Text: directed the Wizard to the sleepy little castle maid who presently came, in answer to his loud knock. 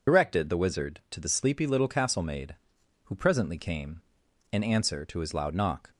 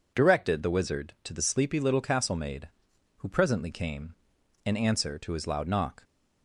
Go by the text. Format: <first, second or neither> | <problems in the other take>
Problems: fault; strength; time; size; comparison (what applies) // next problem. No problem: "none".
second | loses the start of "directed"; at 0.0 s; 55 ms